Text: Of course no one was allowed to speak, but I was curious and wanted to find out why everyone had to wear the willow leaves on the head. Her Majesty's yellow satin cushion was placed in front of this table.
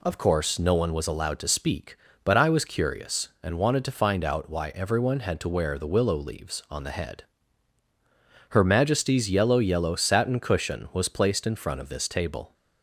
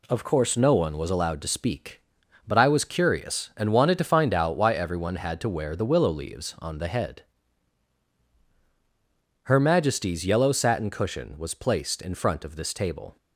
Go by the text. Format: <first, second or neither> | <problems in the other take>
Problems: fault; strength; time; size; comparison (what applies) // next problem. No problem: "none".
second | says "yellow" twice; at 9.5 s